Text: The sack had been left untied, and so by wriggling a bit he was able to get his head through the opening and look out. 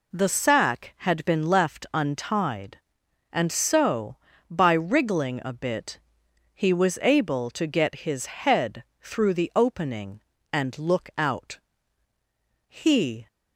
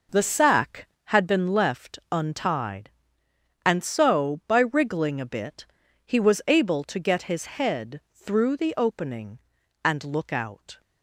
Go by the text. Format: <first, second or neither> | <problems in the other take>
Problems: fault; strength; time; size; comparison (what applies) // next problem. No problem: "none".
second | pauses between "bit" and "he"; noticeable; at 6.0 s; 0.52 s long; also in the second // pauses between "head" and "through"; slight; at 8.8 s; 0.18 s long // goes on to say "He"; from 12.6 s on; 0.60 s long